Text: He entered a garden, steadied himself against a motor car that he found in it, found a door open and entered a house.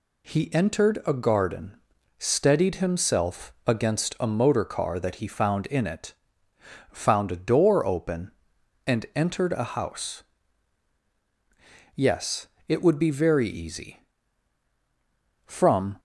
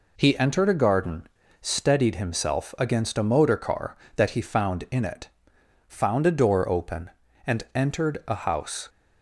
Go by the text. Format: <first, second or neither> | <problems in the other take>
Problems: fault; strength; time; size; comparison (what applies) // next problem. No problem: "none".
second | goes on to say "Yes it would be very easy From"; strong; from 11.9 s on; 4.0 s long